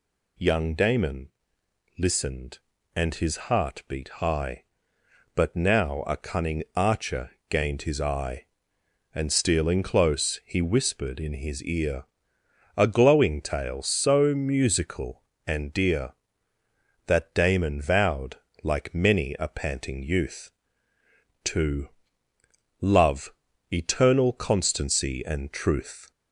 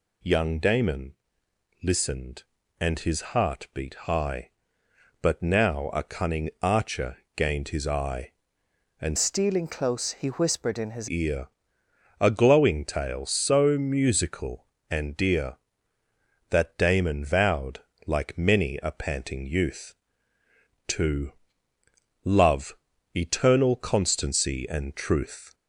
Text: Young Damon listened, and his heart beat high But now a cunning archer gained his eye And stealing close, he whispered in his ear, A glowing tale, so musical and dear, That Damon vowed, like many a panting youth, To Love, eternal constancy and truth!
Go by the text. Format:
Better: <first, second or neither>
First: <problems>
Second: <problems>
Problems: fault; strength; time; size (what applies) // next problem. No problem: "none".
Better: first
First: pauses between "Damon" and "listened"; noticeable; at 1.3 s; 0.68 s long // pauses between "archer" and "gained"; slight; at 7.3 s; 0.18 s long // pauses between "To" and "Love"; noticeable; at 21.8 s; 0.92 s long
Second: pauses between "Damon" and "listened"; noticeable; at 1.1 s; 0.68 s long // pauses between "archer" and "gained"; slight; at 7.1 s; 0.18 s long // changes voice from "stealing" to "his"; from 9.1 to 11.0 s; 1.9 s long // pauses between "To" and "Love"; noticeable; at 21.3 s; 0.92 s long